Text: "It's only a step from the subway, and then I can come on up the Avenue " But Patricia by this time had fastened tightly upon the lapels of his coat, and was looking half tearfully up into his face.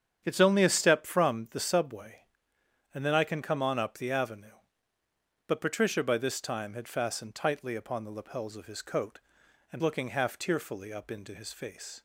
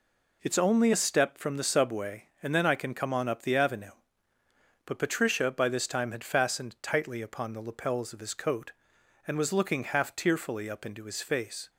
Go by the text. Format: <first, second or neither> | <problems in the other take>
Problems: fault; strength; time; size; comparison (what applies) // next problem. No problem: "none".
second | starts louder than the rest; strong; until 1.2 s; 9 dB // skips "was"; at 9.8 s